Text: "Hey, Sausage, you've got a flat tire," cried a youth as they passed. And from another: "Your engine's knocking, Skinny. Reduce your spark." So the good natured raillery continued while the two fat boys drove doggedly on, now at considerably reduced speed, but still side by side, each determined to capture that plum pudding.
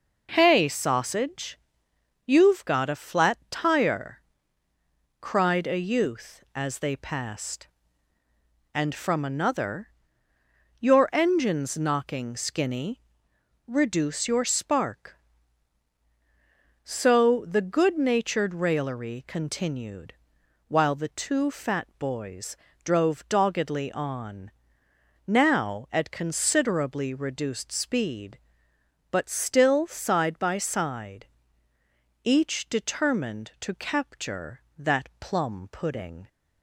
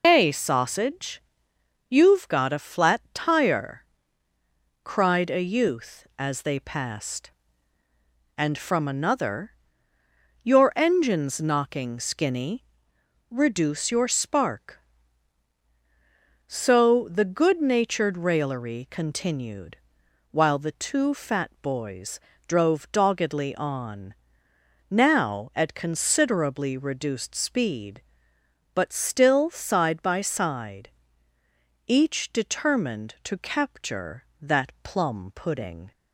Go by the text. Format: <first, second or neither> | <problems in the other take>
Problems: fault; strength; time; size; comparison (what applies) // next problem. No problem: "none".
first | loses the start of "Hey"; at 0.0 s; 125 ms // pauses between "continued" and "while"; noticeable; at 19.7 s; 0.54 s long; noticeable in the first // pauses between "boys" and "drove"; slight; at 22.1 s; 0.28 s long; slight in the first